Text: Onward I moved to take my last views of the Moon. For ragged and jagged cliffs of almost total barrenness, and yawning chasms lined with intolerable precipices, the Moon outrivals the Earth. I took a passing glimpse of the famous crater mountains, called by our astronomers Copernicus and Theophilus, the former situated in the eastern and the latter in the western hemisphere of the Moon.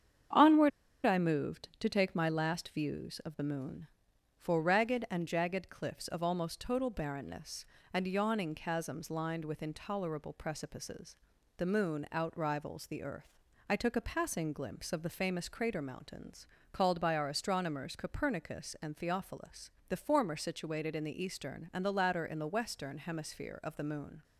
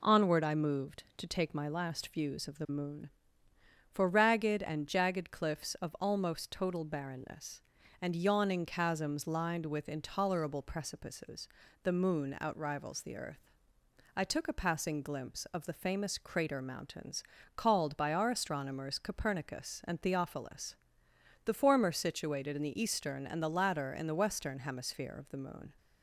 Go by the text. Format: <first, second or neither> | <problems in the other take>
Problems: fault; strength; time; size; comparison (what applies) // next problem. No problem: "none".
second | starts louder than the rest; strong; until 1.6 s; 8 dB // pauses between "Onward" and "I"; slight; at 0.7 s; 0.35 s long